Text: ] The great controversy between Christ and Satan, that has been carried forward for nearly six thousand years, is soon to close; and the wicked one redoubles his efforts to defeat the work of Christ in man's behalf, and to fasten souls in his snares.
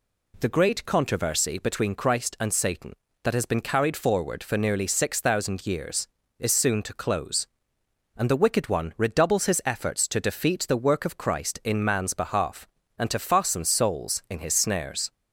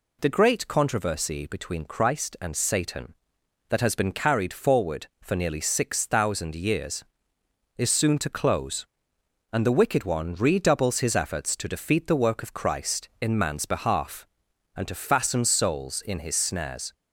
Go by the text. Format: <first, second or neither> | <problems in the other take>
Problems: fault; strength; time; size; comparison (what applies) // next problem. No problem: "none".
neither | none